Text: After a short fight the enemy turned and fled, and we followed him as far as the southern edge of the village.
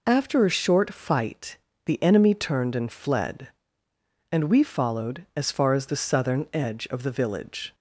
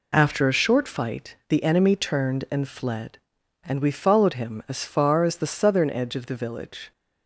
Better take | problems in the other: second | pauses between "fight" and "the"; slight; at 1.5 s; 0.26 s long // skips "him"; at 5.3 s

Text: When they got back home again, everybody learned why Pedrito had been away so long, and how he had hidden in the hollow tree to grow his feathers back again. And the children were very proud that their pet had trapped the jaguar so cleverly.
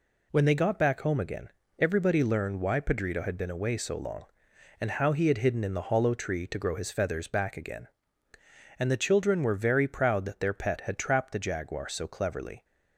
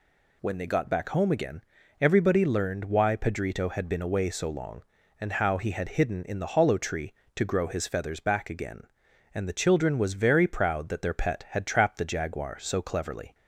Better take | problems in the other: first | says "was" for "were"; at 9.9 s

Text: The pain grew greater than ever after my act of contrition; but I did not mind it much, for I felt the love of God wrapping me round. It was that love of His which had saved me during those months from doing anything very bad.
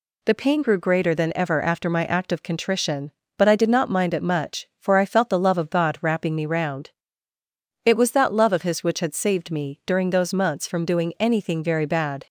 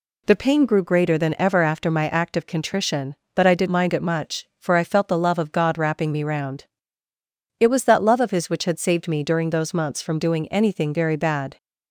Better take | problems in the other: first | skips "not"; at 3.6 s

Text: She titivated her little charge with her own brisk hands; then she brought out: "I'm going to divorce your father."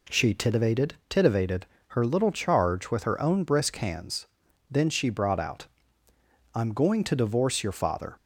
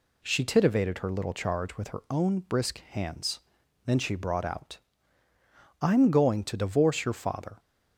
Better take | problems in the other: second | says "titivated" twice; at 1.0 s

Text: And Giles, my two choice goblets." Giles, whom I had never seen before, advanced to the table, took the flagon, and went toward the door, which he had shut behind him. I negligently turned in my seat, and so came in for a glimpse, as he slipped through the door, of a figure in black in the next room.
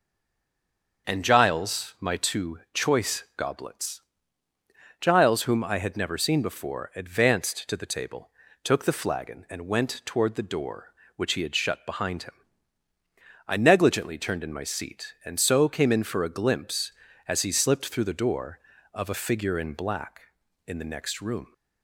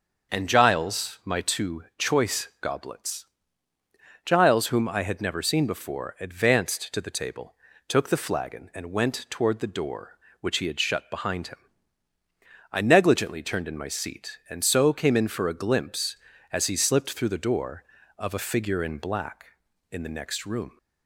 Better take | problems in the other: second | stays silent before the first word; until 1.0 s; 1.0 s long // starts louder than the rest; until 2.1 s; 6.5 dB; also in the second

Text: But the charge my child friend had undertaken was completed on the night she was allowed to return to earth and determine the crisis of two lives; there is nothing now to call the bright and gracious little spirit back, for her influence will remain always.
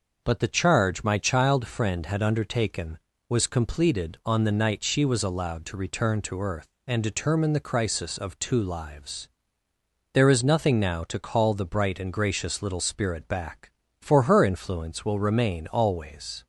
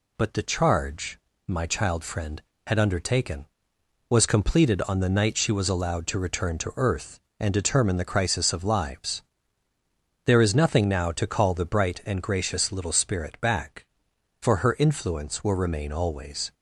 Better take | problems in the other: first | pauses between "charge" and "my"; slight; at 1.1 s; 0.28 s long // skips "two"; at 8.6 s

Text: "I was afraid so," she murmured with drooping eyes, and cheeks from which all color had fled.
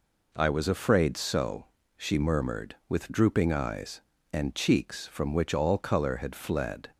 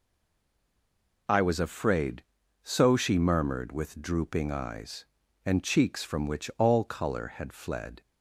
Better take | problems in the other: first | stays silent before the first word; noticeable; until 1.2 s; 1.2 s long

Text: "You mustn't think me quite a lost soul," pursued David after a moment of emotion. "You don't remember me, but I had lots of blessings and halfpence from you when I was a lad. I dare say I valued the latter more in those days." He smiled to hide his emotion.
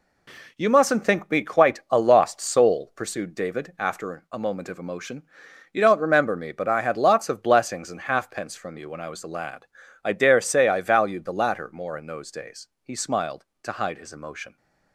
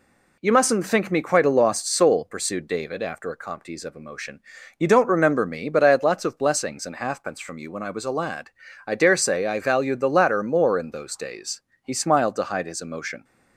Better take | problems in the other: first | says "comptes" for "moment"; at 3.3 s

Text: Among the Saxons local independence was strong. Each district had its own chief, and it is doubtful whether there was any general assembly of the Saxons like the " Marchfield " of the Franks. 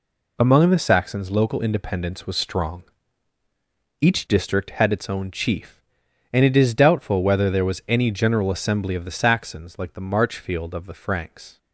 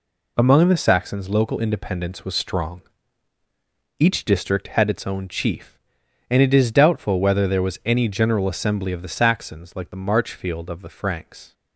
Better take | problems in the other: neither | none

